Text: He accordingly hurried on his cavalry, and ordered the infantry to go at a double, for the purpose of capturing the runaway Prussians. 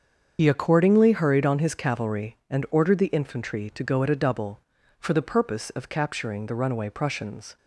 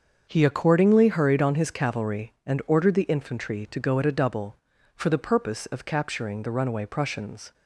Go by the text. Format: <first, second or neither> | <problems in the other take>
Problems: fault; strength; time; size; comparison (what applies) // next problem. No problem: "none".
second | loses the start of "He"; at 0.3 s; 65 ms // starts louder than the rest; strong; until 1.4 s; 7 dB; also in the second